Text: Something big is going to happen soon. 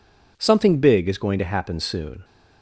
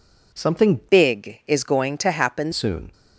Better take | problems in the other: first | changes voice from "big" to "happen"; from 0.9 to 2.5 s; 1.6 s long

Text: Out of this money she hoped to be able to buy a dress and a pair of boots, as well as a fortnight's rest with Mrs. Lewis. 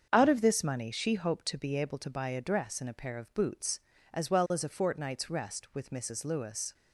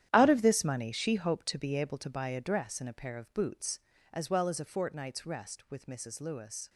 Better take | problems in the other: first | gets quieter; strong; throughout; 13.5 dB // starts louder than the rest; strong; until 1.1 s; 11 dB; strong in the first

